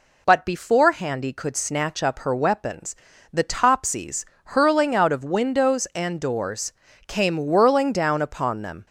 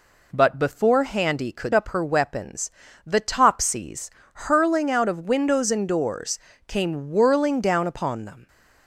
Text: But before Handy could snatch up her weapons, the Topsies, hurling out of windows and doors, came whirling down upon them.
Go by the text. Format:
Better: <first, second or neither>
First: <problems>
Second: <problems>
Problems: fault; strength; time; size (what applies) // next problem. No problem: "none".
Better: first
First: none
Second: skips "snatch"; at 1.7 s